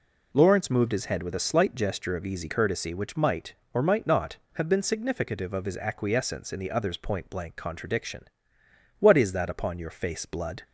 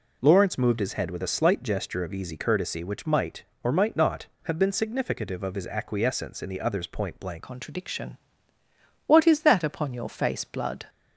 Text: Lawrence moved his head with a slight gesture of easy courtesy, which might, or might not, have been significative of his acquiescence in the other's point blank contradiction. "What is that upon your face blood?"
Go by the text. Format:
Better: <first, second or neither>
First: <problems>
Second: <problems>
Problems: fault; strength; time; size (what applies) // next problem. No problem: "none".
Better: first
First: none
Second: changes voice at "contradiction"; from 7.4 s on; 3.4 s long